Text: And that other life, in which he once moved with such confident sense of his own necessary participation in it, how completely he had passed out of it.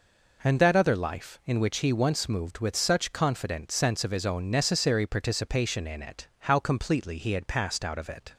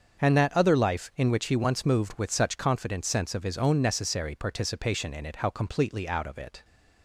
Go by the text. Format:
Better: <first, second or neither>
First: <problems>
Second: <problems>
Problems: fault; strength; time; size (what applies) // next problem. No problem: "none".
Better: first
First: none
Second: starts louder than the rest; until 1.2 s; 7 dB // skips "he had passed"; at 6.0 s